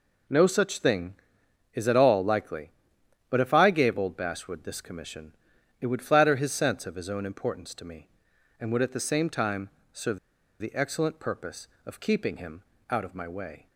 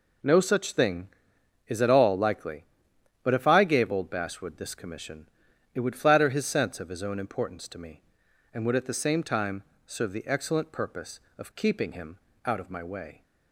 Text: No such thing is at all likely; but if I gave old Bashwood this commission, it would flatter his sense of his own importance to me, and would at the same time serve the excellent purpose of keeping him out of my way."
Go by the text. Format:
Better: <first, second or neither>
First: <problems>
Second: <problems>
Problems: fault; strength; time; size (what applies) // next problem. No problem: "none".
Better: second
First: pauses between "time" and "serve"; slight; at 9.6 s; 0.24 s long // pauses between "serve" and "the"; at 10.1 s; 0.43 s long // pauses between "him" and "out"; slight; at 12.6 s; 0.26 s long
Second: pauses between "time" and "serve"; slight; at 9.6 s; 0.24 s long // pauses between "him" and "out"; slight; at 12.1 s; 0.26 s long